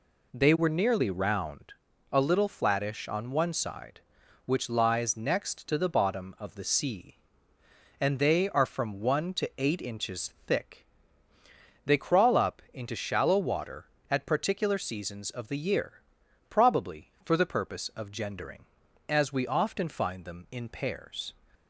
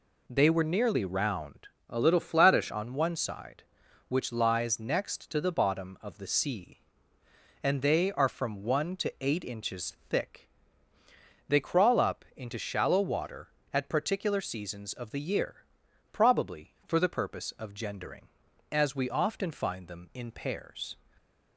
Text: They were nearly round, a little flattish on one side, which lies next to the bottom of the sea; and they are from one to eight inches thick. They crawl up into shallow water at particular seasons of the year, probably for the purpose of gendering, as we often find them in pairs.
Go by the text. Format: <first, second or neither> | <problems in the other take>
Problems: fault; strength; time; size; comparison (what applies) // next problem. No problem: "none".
first | changes voice from "a" to "flattish"; from 1.8 to 2.7 s; 0.9 s long